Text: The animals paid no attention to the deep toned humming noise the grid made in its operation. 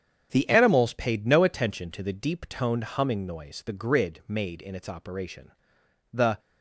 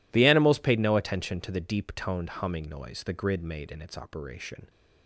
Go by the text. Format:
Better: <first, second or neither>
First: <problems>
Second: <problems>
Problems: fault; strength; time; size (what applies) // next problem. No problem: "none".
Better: second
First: starts louder than the rest; strong; until 1.3 s; 7.5 dB // goes on to say "The"; slight; from 6.1 s on; 0.26 s long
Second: none